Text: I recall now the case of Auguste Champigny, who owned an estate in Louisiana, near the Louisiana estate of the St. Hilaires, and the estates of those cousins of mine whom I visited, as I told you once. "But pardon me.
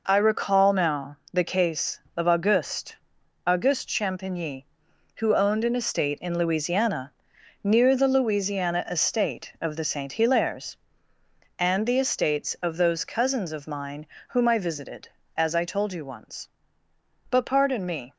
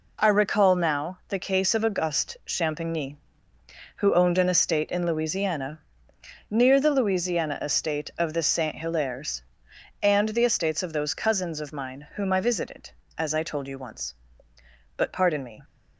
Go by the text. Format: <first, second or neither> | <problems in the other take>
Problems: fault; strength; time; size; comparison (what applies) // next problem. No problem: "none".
second | pauses between "now" and "the"; slight; at 1.1 s; 0.16 s long // says "Auguste" twice; at 3.4 s // pauses between "mine" and "whom"; slight; at 14.0 s; 0.22 s long